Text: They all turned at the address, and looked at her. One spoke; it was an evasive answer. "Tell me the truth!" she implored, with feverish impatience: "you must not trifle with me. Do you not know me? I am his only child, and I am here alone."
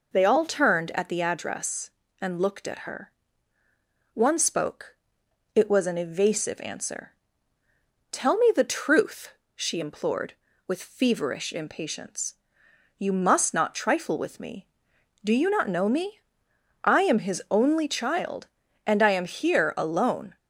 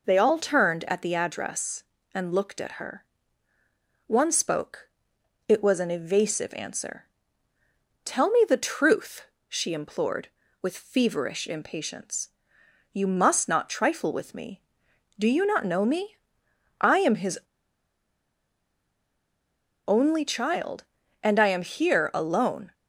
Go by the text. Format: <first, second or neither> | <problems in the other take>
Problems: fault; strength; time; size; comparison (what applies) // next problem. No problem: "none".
first | pauses between "his" and "only"; strong; at 17.3 s; 2.4 s long